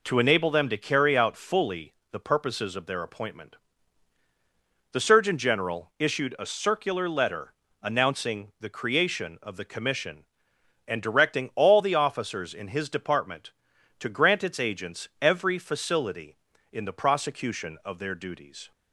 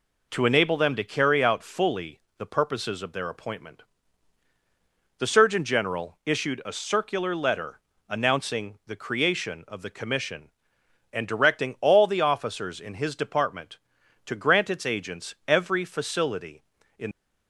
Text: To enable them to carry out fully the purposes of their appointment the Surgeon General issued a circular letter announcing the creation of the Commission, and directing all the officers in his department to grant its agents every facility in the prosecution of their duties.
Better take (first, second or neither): first